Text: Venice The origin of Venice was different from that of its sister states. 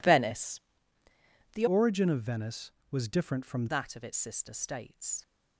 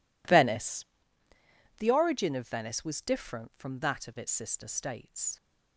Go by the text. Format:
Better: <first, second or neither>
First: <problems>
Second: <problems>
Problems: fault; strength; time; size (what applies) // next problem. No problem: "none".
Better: second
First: pauses between "Venice" and "The"; noticeable; at 0.5 s; 0.94 s long // changes voice from "origin" to "from"; from 1.6 to 3.6 s; 2.0 s long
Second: pauses between "Venice" and "The"; noticeable; at 0.8 s; 0.94 s long